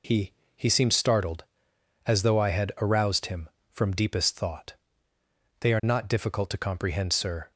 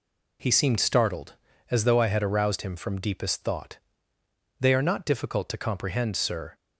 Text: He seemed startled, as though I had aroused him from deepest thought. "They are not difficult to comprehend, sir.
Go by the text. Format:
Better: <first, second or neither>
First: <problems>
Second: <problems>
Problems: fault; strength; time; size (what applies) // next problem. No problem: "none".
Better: second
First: says "He" twice; at 0.5 s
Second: none